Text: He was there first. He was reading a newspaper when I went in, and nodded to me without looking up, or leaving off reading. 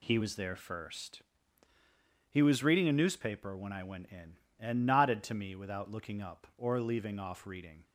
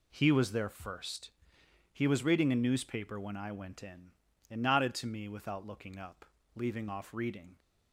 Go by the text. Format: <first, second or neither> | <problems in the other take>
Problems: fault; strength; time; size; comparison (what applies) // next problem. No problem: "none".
first | skips "or"; at 6.4 s